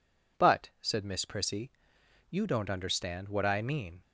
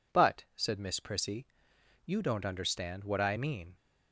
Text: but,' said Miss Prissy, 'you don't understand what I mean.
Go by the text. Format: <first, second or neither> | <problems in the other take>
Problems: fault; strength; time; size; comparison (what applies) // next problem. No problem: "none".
neither | none